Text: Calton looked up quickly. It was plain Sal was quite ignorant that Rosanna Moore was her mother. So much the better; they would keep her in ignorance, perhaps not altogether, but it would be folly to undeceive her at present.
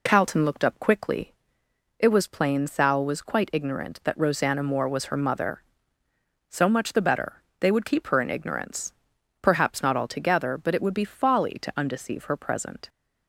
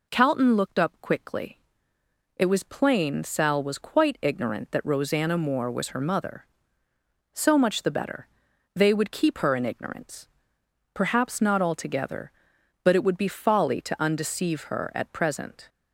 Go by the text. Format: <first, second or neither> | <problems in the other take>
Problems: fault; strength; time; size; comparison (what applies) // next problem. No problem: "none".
second | skips "at"; at 12.3 s